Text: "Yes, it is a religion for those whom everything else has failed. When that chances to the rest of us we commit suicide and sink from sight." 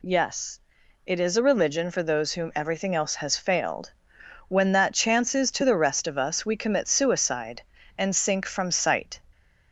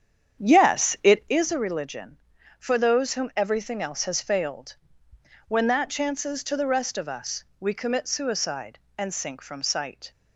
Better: first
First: none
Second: starts louder than the rest; strong; until 1.5 s; 8.5 dB // pauses between "us" and "we"; slight; at 7.4 s; 0.16 s long

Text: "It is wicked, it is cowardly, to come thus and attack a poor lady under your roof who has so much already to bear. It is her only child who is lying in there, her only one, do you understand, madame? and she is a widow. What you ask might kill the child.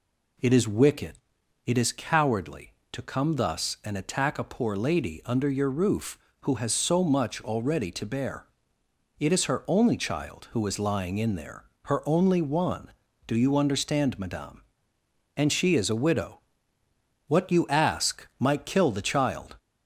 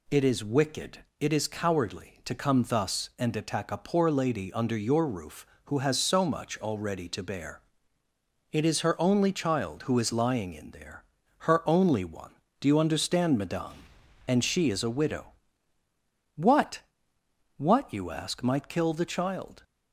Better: first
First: none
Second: says "What" twice; at 17.5 s

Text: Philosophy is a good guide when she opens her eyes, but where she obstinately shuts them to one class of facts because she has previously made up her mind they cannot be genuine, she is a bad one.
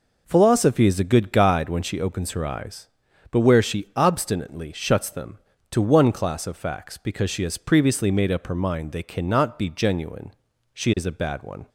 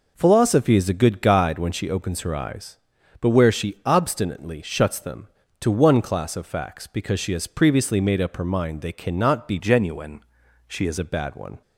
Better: first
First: none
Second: changes voice from "genuine" to "is"; from 9.5 to 10.9 s; 1.4 s long

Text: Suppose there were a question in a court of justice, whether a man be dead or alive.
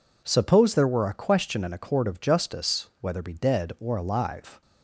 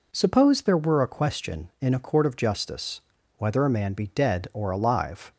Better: second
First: skips "a man"; at 3.2 s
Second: none

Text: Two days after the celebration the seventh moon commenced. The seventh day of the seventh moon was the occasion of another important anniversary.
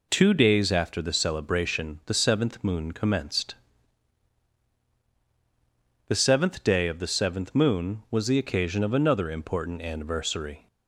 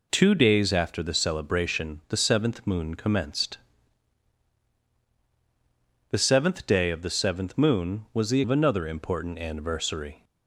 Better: first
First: none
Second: skips "occasion"; at 8.4 s

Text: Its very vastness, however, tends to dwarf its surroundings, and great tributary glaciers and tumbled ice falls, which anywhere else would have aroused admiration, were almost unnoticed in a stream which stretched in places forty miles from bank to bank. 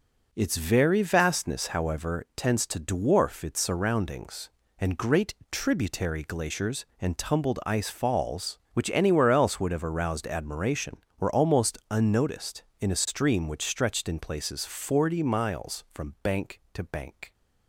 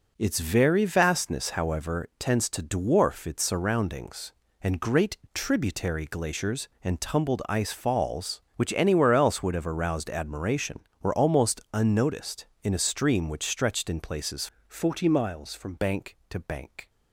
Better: first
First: pauses between "great" and "tributary"; slight; at 5.3 s; 0.18 s long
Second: pauses between "great" and "tributary"; slight; at 5.1 s; 0.18 s long // changes voice from "forty" to "from"; from 14.6 to 15.7 s; 1.1 s long

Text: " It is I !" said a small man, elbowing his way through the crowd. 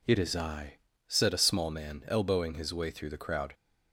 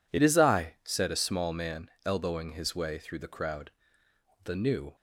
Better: first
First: none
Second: goes on to say "The new"; from 4.4 s on; 0.50 s long

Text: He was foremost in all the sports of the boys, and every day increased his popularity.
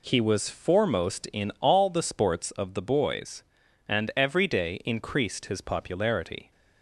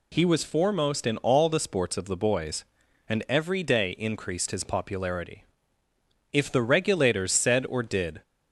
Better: first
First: none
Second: goes on to say "If the Regulators said or did"; strong; from 6.3 s on; 1.9 s long

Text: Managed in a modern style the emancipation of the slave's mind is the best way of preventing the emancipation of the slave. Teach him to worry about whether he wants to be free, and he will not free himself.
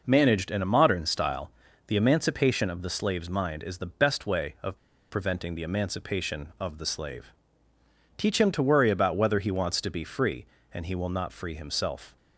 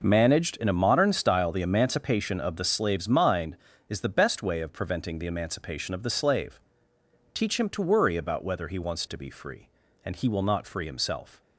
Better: second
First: pauses between "style" and "the"; at 1.4 s; 0.38 s long // pauses between "of" and "preventing"; slight; at 4.7 s; 0.32 s long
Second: none

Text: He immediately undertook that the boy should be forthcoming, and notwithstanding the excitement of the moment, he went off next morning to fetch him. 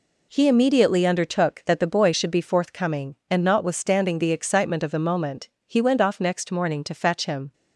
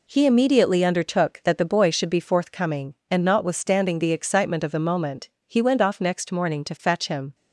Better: neither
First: none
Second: none

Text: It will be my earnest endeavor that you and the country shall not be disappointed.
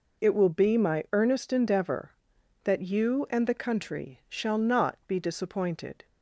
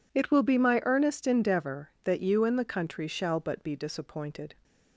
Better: first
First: none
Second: says "but" for "not"; at 3.3 s

